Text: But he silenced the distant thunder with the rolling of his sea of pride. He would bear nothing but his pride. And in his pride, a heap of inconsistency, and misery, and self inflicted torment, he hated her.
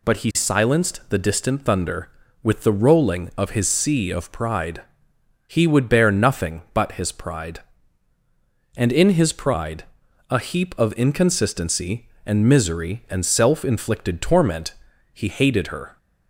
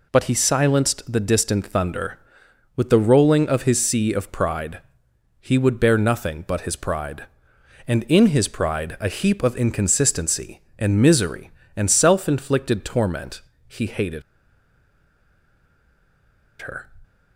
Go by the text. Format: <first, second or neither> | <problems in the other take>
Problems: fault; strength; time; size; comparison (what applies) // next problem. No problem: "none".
first | pauses between "hated" and "her"; strong; at 14.2 s; 2.3 s long